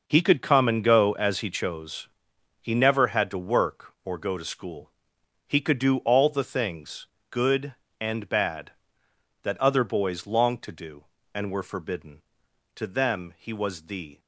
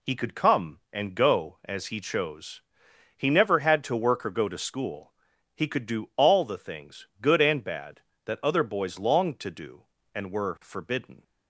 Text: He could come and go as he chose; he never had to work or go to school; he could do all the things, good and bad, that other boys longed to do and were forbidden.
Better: second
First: goes on to say "To them he was the"; from 12.7 s on; 1.4 s long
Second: none

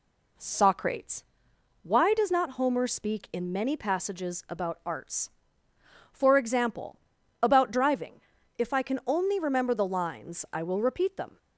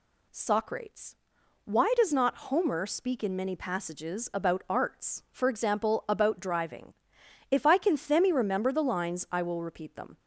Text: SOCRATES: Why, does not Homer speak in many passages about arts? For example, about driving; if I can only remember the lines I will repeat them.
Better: first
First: none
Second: says "themi" for "only"; at 7.9 s

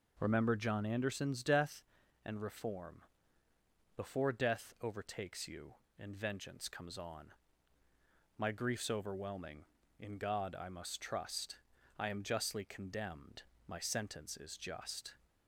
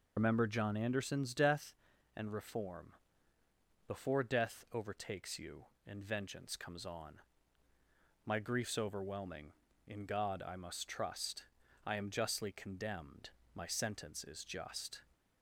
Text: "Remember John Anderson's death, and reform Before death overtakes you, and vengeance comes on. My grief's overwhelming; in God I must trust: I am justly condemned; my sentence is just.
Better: first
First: pauses between "reform" and "Before"; noticeable; at 3.0 s; 0.94 s long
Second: loses the start of "Remember"; at 0.1 s; 90 ms // pauses between "reform" and "Before"; noticeable; at 2.9 s; 0.94 s long

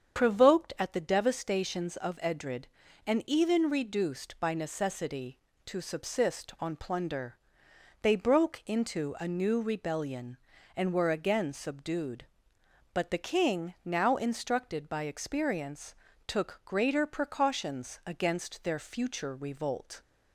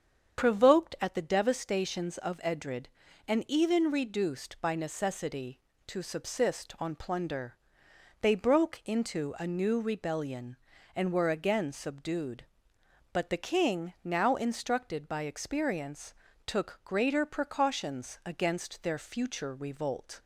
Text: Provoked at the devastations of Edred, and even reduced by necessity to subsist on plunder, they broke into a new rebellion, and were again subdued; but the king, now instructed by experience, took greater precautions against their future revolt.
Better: neither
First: starts louder than the rest; strong; until 1.2 s; 7.5 dB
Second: starts louder than the rest; strong; until 1.4 s; 7.5 dB

